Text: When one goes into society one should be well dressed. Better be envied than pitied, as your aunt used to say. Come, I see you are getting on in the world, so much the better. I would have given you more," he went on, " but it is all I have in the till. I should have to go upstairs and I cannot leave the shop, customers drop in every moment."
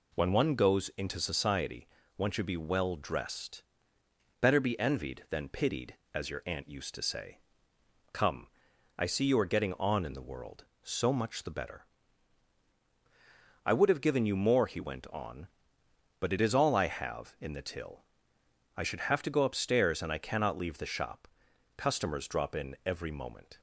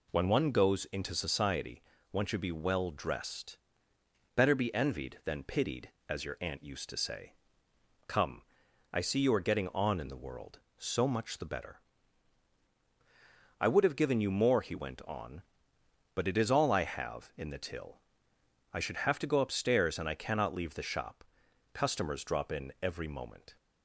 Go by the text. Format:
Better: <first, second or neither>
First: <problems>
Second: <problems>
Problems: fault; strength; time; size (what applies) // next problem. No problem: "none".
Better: neither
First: pauses between "society" and "one"; slight; at 1.8 s; 0.30 s long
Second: pauses between "society" and "one"; slight; at 1.8 s; 0.30 s long